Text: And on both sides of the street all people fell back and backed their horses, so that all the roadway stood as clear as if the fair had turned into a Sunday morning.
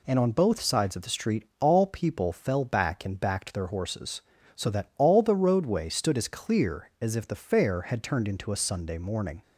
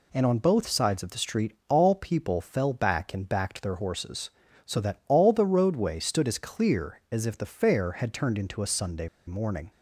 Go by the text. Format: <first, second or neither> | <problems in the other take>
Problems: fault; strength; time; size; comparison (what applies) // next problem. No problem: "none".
first | pauses between "street" and "all"; slight; at 1.5 s; 0.16 s long; slight in the first // pauses between "Sunday" and "morning"; slight; at 9.0 s; 0.19 s long